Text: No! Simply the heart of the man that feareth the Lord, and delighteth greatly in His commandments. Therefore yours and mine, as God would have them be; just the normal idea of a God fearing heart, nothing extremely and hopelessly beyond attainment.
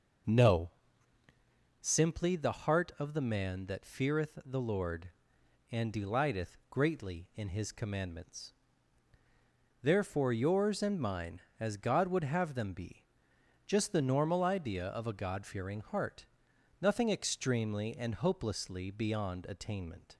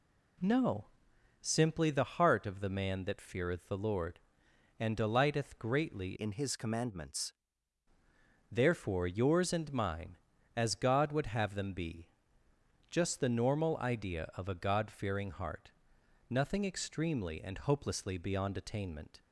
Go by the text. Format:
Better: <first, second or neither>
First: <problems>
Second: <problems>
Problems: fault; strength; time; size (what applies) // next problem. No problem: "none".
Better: first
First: none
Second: changes voice from "in" to "commandments"; from 6.1 to 7.3 s; 1.2 s long